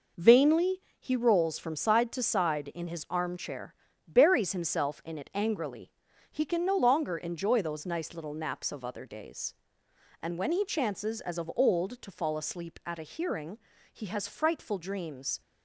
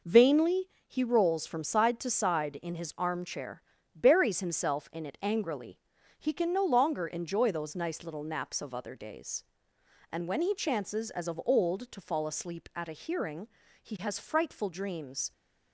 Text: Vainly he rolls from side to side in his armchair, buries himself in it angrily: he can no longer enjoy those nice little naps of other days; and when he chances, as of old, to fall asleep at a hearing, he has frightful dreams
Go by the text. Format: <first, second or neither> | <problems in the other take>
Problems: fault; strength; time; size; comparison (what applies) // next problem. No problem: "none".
neither | pauses between "Vainly" and "he"; slight; the same in both